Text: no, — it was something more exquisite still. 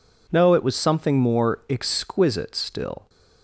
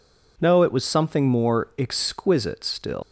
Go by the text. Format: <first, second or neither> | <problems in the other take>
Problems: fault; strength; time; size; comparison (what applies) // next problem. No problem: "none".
first | leaves "still" unfinished; at 3.0 s; 155 ms